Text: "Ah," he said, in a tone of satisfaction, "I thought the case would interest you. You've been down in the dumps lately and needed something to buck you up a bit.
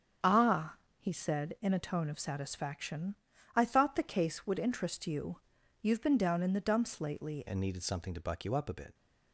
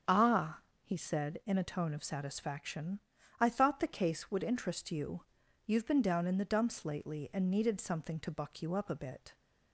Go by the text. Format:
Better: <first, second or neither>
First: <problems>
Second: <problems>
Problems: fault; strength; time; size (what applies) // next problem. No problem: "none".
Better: second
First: starts louder than the rest; strong; until 1.4 s; 7.5 dB // changes voice at "and"; from 7.4 s on; 1.5 s long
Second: starts louder than the rest; strong; until 1.3 s; 7.5 dB